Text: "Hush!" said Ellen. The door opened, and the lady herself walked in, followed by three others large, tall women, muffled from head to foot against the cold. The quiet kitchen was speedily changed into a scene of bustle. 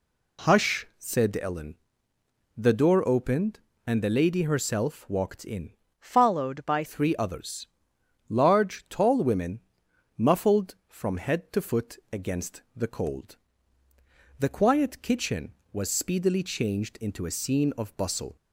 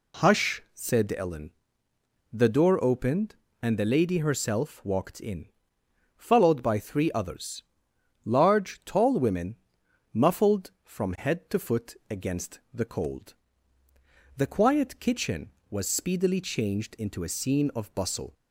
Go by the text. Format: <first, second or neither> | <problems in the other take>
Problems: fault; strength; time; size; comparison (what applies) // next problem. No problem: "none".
second | changes voice from "followed" to "by"; from 5.9 to 6.8 s; 0.9 s long // pauses between "others" and "large"; noticeable; at 7.6 s; 0.60 s long; noticeable in the second // pauses between "against" and "the"; slight; at 12.5 s; 0.16 s long; slight in the second